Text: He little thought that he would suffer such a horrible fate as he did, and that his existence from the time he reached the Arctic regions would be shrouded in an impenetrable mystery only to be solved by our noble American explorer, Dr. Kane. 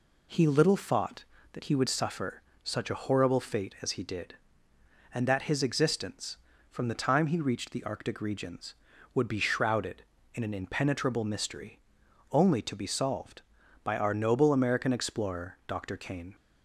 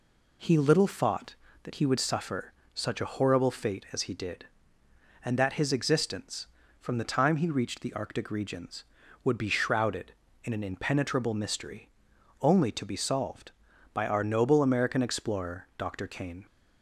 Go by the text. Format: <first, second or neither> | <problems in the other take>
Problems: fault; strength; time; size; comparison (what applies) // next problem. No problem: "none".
neither | pauses between "suffer" and "such"; slight; the same in both // pauses between "mystery" and "only"; noticeable; the same in both